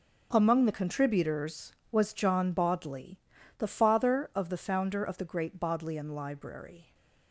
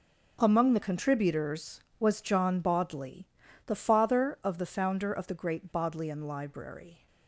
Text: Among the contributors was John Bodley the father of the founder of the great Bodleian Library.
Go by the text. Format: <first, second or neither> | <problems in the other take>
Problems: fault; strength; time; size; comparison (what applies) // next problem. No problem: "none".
neither | pauses between "Bodley" and "the"; the same in both